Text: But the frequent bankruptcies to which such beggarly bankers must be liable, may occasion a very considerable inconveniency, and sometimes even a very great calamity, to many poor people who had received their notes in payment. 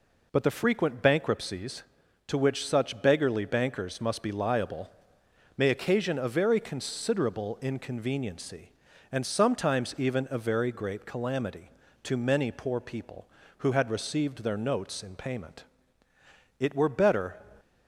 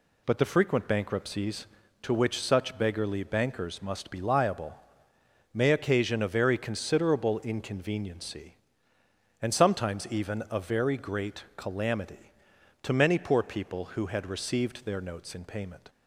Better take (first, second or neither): second